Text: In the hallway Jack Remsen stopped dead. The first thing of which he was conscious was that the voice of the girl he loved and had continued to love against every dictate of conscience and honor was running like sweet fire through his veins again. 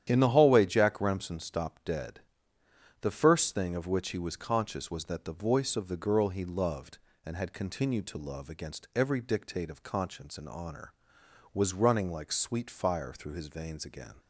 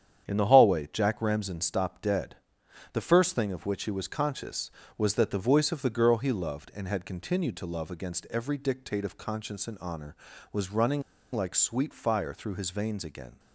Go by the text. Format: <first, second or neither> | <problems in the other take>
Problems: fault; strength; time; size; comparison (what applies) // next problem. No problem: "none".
first | starts louder than the rest; strong; until 1.2 s; 9 dB; strong in the first // pauses between "running" and "like"; slight; at 11.0 s; 0.32 s long